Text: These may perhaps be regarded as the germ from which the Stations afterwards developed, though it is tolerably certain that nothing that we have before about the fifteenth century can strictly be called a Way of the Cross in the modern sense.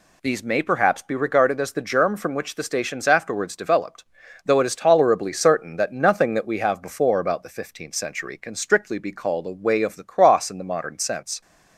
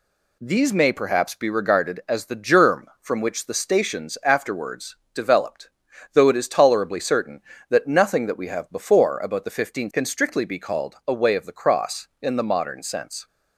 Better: first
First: none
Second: pauses between "afterwards" and "developed"; slight; at 4.9 s; 0.18 s long // skips "century"; at 9.9 s

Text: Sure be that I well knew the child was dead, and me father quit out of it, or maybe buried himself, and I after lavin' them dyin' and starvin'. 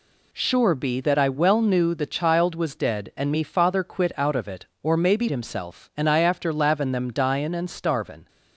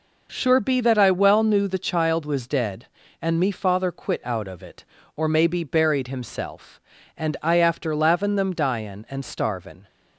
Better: second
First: skips "buried"; at 5.2 s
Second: none

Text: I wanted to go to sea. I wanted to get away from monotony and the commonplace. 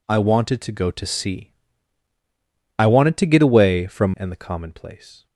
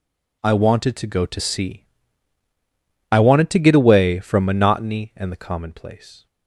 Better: second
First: skips "monotony"; at 4.1 s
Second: none

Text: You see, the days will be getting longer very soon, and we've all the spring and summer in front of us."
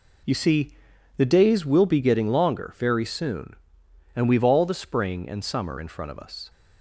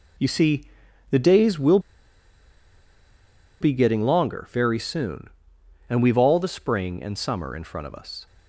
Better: first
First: none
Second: pauses between "will" and "be"; strong; at 1.7 s; 1.8 s long

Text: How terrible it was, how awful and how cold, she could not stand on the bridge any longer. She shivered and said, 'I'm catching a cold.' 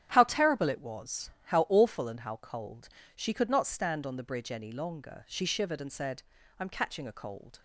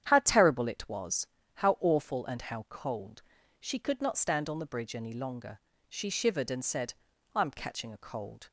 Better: neither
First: starts louder than the rest; strong; until 1.1 s; 11 dB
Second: starts louder than the rest; strong; until 1.0 s; 9.5 dB

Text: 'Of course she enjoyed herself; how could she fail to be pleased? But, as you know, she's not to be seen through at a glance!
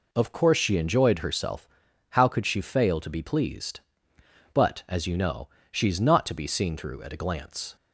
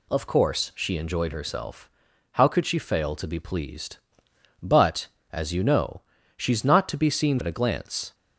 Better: first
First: none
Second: skips "through"; at 7.3 s

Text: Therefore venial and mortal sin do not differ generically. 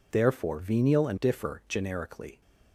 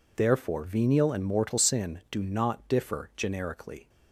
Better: second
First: skips "mortal sin do not"; at 1.1 s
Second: none

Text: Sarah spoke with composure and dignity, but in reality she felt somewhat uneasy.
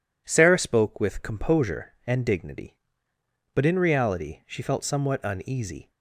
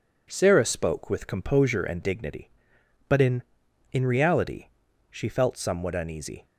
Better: first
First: none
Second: says "in" twice; at 3.9 s // pauses between "reality" and "she"; at 4.6 s; 0.42 s long

